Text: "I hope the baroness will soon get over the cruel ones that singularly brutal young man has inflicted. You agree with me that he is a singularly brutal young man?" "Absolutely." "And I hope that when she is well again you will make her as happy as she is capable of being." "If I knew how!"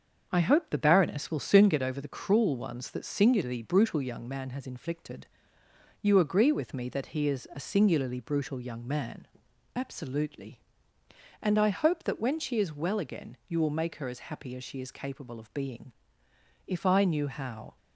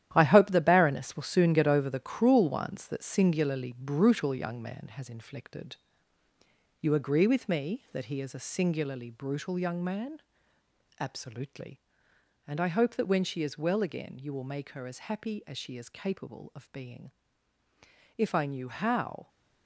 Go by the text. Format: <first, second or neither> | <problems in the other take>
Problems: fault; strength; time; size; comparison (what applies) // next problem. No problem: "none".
first | gets quieter; strong; throughout; 9.5 dB // starts louder than the rest; strong; until 1.1 s; 11.5 dB; also in the first